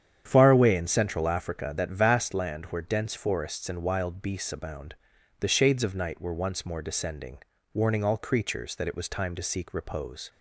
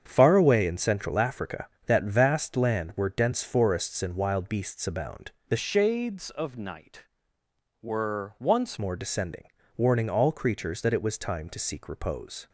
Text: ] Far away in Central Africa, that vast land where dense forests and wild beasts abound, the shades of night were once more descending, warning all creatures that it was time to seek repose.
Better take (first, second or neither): first